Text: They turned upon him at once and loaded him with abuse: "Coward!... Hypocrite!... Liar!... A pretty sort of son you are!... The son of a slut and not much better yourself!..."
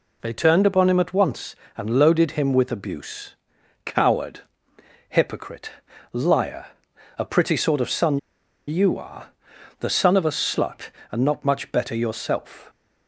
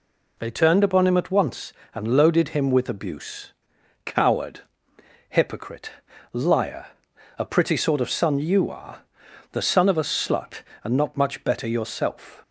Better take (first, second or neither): second